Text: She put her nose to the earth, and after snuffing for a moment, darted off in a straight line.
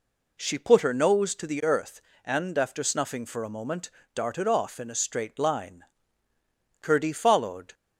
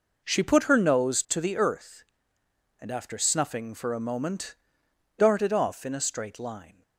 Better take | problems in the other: second | goes on to say "Curdie followed"; noticeable; from 6.7 s on; 0.94 s long

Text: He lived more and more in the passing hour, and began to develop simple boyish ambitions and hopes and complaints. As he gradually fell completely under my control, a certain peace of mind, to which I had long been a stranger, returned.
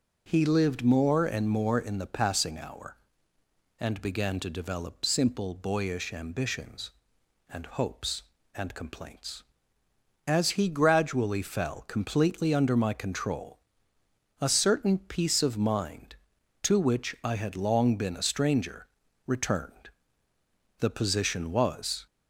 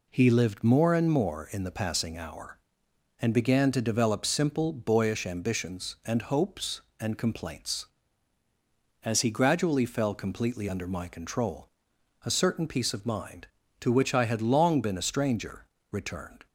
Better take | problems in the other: second | goes on to say "The position was"; noticeable; from 20.7 s on; 1.2 s long

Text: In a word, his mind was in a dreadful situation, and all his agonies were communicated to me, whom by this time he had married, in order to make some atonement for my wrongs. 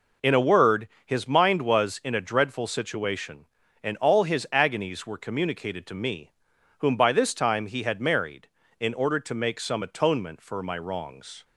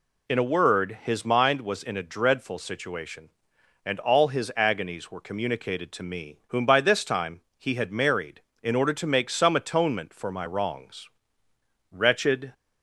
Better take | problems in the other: first | pauses between "time" and "he"; slight; at 7.4 s; 0.18 s long // goes on to say "Wretched"; noticeable; from 11.9 s on; 0.62 s long

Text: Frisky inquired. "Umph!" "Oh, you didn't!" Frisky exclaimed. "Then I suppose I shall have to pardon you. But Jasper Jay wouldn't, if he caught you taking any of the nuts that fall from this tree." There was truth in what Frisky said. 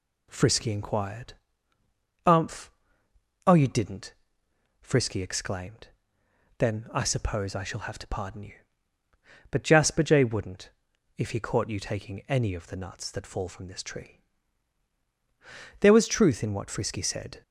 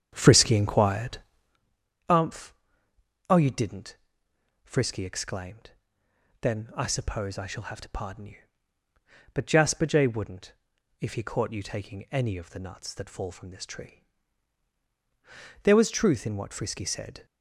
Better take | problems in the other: first | starts louder than the rest; strong; until 1.6 s; 8.5 dB

